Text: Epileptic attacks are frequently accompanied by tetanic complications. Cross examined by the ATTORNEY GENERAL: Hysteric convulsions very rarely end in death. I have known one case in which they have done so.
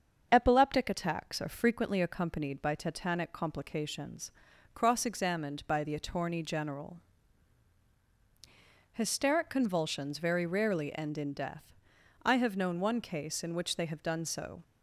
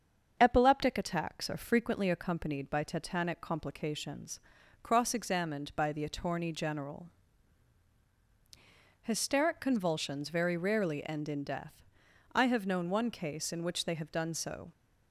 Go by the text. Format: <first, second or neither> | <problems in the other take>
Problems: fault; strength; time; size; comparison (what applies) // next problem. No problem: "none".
neither | starts louder than the rest; the same in both